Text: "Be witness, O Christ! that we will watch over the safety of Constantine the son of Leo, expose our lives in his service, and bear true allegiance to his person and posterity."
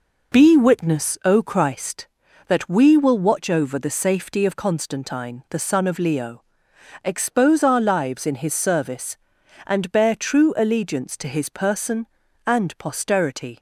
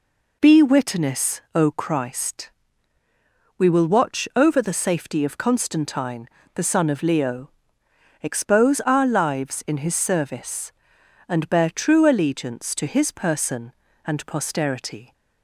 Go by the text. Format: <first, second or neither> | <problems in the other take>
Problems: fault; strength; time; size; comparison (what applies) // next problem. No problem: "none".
first | skips "that"; at 3.0 s // pauses between "Constantine" and "the"; slight; at 6.2 s; 0.26 s long